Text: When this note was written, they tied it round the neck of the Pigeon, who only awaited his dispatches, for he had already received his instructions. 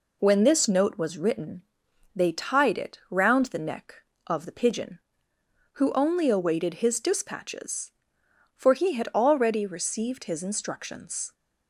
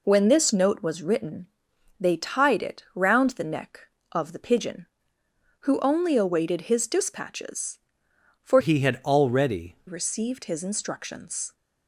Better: first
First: none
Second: changes voice from "he" to "already"; from 8.6 to 9.7 s; 1.1 s long

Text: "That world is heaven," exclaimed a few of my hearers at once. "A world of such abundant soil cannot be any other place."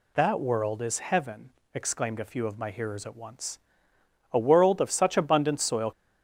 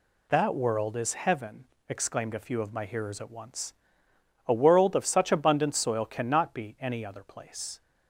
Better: second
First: stops before "cannot be any other place"; at 5.9 s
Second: none

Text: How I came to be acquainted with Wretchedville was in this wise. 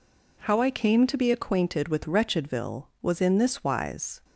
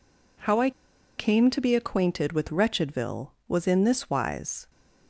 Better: first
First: none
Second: pauses between "I" and "came"; noticeable; at 0.7 s; 0.47 s long

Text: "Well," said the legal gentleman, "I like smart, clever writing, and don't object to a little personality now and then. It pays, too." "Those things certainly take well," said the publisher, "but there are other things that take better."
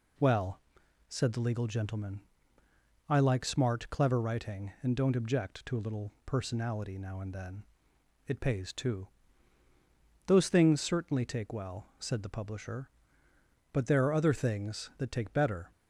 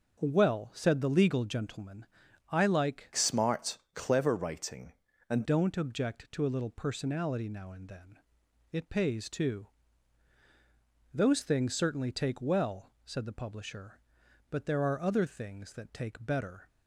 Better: first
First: none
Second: changes voice from "smart" to "and"; from 3.1 to 5.4 s; 2.3 s long

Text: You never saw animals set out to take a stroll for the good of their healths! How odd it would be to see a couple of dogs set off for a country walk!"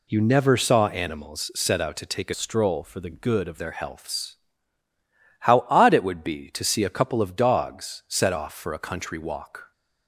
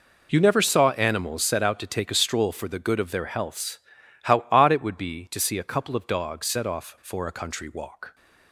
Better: second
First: changes voice from "stroll" to "of"; from 2.3 to 3.5 s; 1.2 s long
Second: none

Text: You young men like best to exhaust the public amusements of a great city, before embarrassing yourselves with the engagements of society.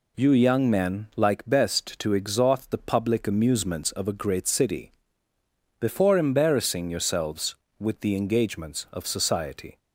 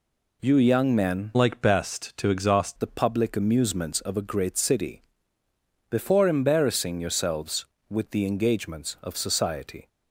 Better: first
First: none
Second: changes voice from "like" to "exhaust"; from 1.3 to 2.7 s; 1.4 s long

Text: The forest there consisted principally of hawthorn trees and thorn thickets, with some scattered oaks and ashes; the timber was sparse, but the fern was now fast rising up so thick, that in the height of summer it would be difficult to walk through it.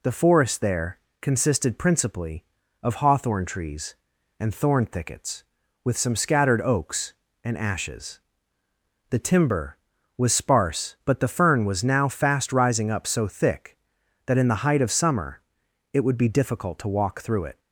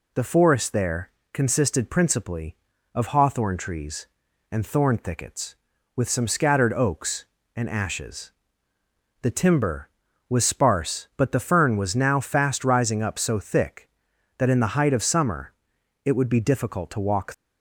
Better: first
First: pauses between "there" and "consisted"; slight; at 0.9 s; 0.22 s long // pauses between "summer" and "it"; noticeable; at 15.4 s; 0.50 s long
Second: pauses between "there" and "consisted"; slight; at 1.1 s; 0.22 s long // pauses between "summer" and "it"; noticeable; at 15.5 s; 0.50 s long // stops before "through it"; at 17.3 s

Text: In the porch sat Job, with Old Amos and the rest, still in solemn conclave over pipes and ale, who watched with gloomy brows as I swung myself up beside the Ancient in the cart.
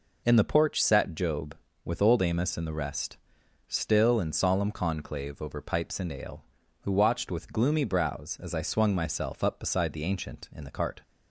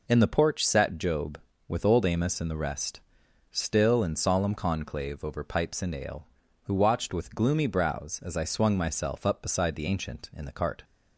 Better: neither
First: none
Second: none

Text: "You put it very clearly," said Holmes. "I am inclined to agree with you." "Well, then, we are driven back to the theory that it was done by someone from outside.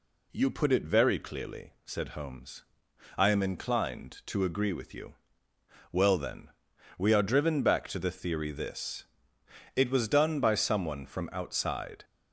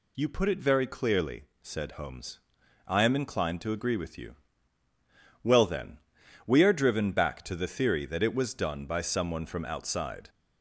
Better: second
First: says "this" for "that"; at 8.5 s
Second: none

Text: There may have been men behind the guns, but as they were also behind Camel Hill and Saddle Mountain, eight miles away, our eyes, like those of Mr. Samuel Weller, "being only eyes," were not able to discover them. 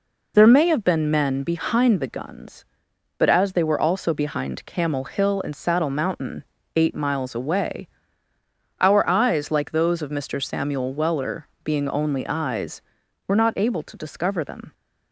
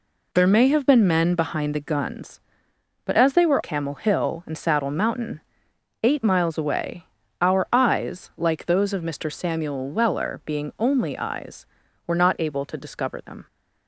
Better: first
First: none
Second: skips "also behind"; at 3.6 s

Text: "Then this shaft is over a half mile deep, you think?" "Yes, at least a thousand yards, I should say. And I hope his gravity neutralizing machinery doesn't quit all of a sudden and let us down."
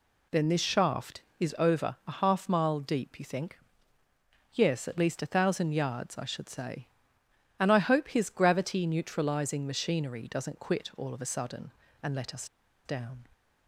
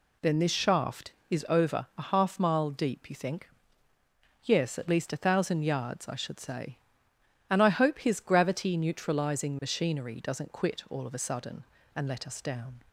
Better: second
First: pauses between "us" and "down"; at 12.4 s; 0.38 s long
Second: none

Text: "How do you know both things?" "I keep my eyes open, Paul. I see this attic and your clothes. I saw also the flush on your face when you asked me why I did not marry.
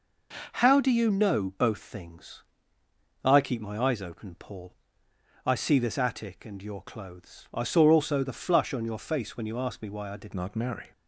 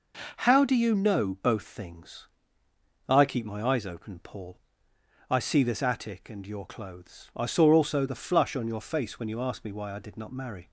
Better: second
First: changes voice at "not"; from 10.3 s on; 0.6 s long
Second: none

